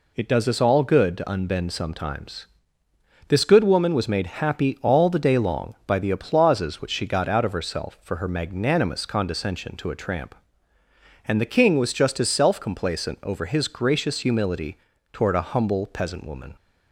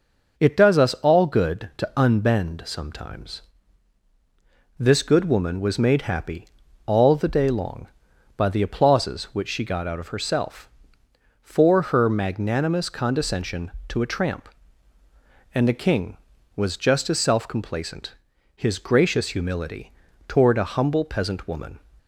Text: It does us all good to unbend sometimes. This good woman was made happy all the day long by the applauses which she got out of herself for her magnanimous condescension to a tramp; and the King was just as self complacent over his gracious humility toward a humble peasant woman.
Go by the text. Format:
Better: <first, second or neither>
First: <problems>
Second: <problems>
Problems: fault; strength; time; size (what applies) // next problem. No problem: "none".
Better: first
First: pauses between "humility" and "toward"; slight; at 14.7 s; 0.34 s long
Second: pauses between "happy" and "all"; at 6.4 s; 0.38 s long // skips "over"; at 18.3 s // pauses between "humility" and "toward"; slight; at 19.9 s; 0.36 s long